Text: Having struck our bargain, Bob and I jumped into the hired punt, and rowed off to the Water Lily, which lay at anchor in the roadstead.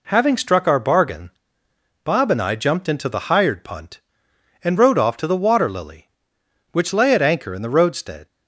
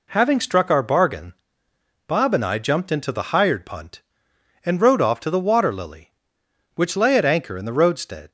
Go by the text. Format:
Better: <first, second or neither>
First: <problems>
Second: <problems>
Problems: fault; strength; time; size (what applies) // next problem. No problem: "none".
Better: neither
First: none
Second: none